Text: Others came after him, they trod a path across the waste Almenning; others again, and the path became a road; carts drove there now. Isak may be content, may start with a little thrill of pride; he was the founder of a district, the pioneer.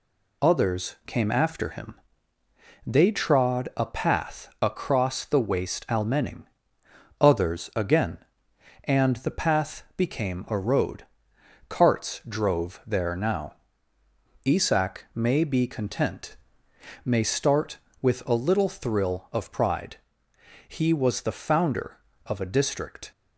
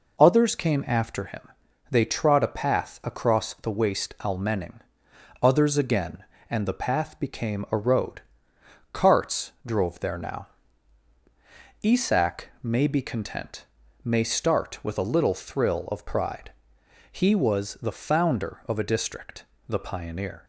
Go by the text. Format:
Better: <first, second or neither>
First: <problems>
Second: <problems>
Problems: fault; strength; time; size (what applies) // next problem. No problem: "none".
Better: second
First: stops before "the pioneer"; at 23.1 s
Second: none